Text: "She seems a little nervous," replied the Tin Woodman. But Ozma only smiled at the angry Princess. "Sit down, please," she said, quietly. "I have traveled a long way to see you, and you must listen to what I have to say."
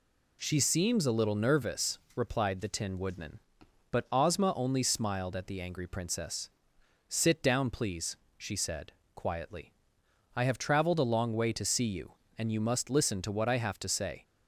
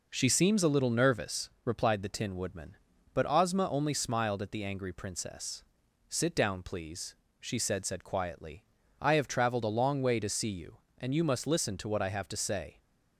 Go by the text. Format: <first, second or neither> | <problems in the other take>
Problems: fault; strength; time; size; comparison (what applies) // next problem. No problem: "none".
first | says "said" twice; at 7.8 s